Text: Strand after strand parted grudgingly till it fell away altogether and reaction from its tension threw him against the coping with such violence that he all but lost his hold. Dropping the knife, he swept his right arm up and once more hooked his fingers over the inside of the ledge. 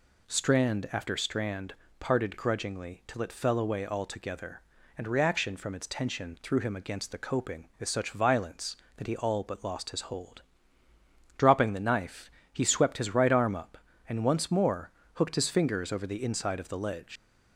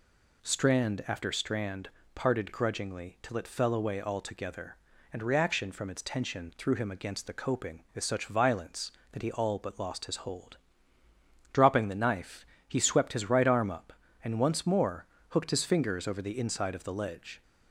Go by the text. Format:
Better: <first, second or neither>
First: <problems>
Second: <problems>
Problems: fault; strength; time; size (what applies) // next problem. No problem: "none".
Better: second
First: pauses between "strand" and "parted"; slight; at 1.7 s; 0.24 s long // pauses between "more" and "hooked"; slight; at 14.9 s; 0.24 s long // leaves "ledge" unfinished; at 17.1 s; 110 ms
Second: pauses between "strand" and "parted"; slight; at 1.8 s; 0.24 s long // pauses between "more" and "hooked"; slight; at 15.0 s; 0.24 s long